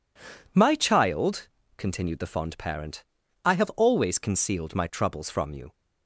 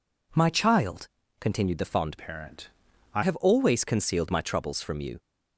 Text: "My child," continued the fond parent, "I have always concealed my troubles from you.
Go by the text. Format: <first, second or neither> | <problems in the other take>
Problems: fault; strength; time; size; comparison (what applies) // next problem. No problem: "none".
first | changes voice from "parent" to "I"; from 2.1 to 3.2 s; 1.1 s long